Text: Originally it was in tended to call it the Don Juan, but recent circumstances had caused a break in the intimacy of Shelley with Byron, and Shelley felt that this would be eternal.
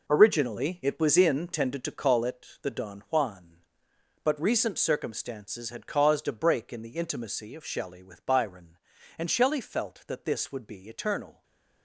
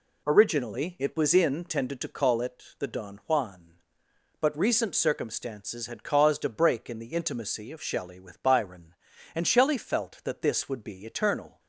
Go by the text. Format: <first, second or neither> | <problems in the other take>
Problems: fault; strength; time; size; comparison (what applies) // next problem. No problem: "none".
second | gets quieter; strong; throughout; 11 dB // pauses between "it" and "the"; slight; at 2.4 s; 0.16 s long; slight in the second // stays silent after the last word; slight; from 11.3 s on; 0.5 s long